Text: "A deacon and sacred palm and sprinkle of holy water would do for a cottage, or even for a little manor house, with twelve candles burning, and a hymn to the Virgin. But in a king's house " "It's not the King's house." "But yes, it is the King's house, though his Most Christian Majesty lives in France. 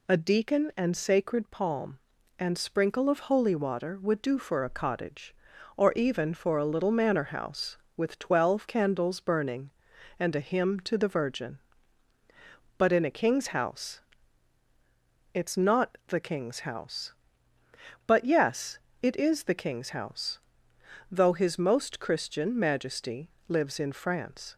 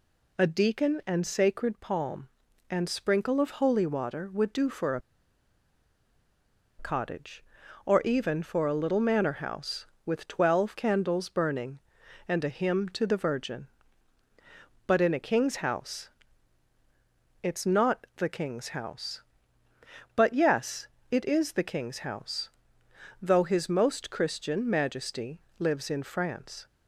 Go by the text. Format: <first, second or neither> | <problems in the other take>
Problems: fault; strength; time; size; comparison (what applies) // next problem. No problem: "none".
first | pauses between "a" and "cottage"; strong; at 4.9 s; 1.7 s long // pauses between "Majesty" and "lives"; slight; at 25.3 s; 0.18 s long; slight in the first